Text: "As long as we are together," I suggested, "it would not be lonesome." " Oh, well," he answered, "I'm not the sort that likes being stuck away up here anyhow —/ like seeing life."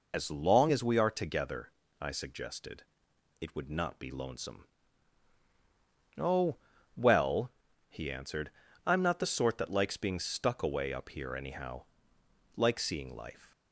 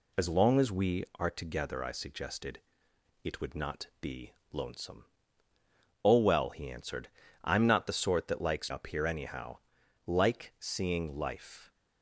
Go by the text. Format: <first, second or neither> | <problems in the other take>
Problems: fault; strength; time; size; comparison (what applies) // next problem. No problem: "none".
first | pauses between "be" and "lonesome"; slight; at 4.3 s; 0.18 s long // skips "being stuck away"; at 8.6 s